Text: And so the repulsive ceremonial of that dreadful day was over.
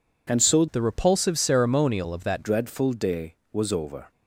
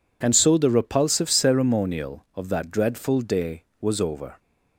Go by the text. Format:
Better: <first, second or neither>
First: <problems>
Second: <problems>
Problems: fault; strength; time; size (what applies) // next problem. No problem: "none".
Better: second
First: changes voice from "the" to "that"; from 0.7 to 2.4 s; 1.7 s long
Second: none